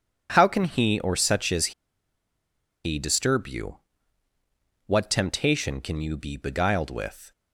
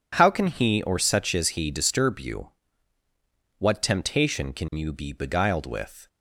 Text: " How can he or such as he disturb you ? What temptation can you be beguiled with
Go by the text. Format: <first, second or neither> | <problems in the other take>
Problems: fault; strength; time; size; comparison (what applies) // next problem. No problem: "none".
second | pauses between "as" and "he"; at 1.7 s; 1.1 s long